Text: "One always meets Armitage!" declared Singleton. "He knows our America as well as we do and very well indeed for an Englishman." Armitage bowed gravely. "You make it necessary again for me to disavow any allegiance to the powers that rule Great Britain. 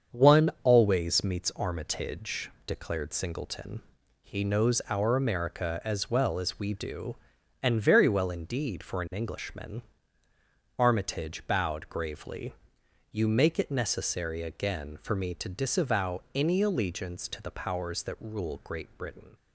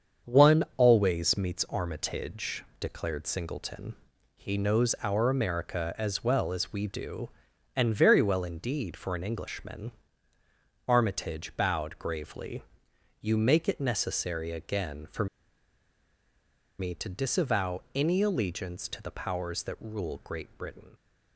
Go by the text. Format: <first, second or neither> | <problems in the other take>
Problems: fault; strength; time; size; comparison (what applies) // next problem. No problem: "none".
first | starts louder than the rest; strong; until 1.4 s; 7 dB; strong in the first // pauses between "for" and "me"; strong; at 15.2 s; 1.5 s long